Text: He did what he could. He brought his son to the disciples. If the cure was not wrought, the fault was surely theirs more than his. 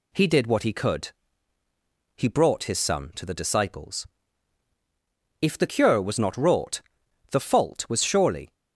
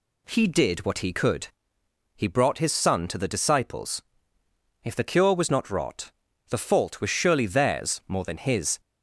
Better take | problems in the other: second | stops before "theirs more than his"; at 8.5 s

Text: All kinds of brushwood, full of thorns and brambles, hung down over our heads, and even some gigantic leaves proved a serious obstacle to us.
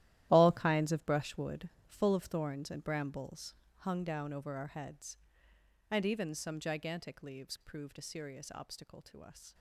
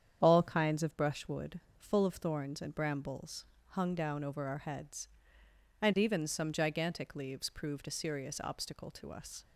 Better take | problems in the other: second | gets quieter; strong; throughout; 13 dB // starts louder than the rest; strong; until 1.3 s; 13.5 dB; strong in the second

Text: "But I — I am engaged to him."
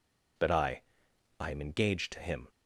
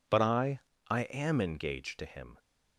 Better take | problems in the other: neither | none

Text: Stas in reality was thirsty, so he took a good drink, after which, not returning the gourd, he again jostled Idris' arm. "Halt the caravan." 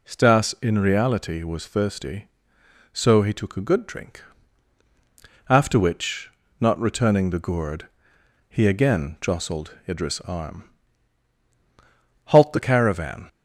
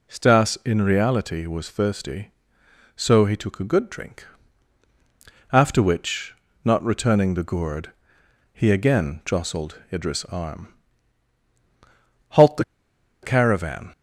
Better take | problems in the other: first | pauses between "the" and "caravan"; noticeable; at 12.6 s; 0.59 s long

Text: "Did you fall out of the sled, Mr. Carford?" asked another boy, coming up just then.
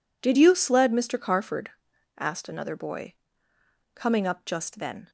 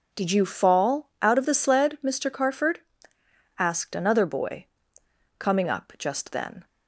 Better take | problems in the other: second | skips "fall out of the"; at 0.5 s

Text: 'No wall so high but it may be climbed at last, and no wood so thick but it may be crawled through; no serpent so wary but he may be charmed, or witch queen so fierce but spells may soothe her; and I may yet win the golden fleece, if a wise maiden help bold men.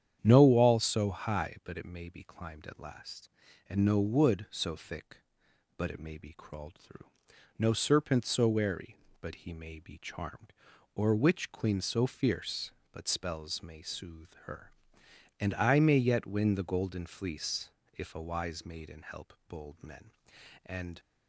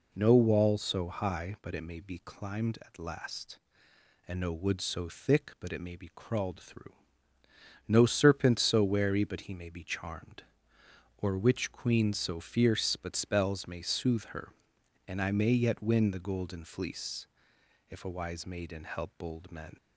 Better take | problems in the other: second | starts louder than the rest; strong; until 1.2 s; 9 dB // goes on to say "And"; slight; from 20.6 s on; 0.34 s long

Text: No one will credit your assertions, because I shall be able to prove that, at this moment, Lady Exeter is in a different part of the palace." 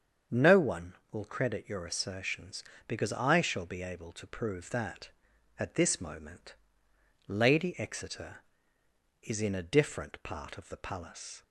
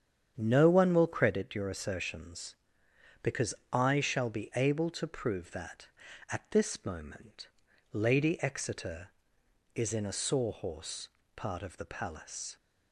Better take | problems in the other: first | starts louder than the rest; strong; until 1.3 s; 8.5 dB; strong in the first // pauses between "because" and "I"; slight; at 3.5 s; 0.18 s long // says "sawhorse" for "different"; at 10.1 s

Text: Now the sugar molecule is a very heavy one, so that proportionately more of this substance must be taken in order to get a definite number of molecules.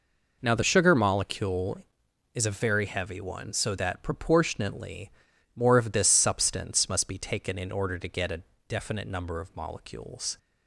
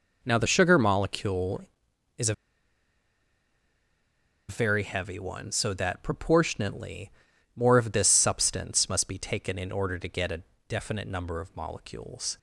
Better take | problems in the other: first | pauses between "a" and "very"; strong; at 2.3 s; 2.1 s long // pauses between "proportionately" and "more"; noticeable; at 7.0 s; 0.46 s long; noticeable in the first // pauses between "a" and "definite"; slight; at 10.4 s; 0.26 s long; slight in the first

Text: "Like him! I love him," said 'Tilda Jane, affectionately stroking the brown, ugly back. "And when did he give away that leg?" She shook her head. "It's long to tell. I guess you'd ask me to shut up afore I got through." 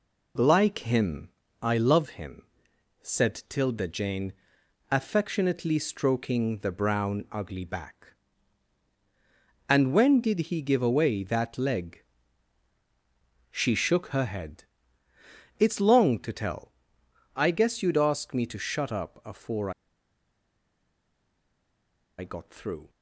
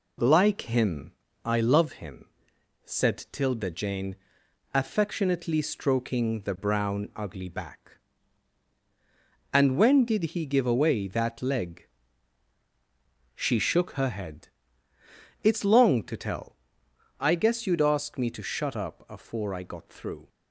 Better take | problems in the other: second | pauses between "afore" and "I"; strong; at 19.7 s; 2.4 s long

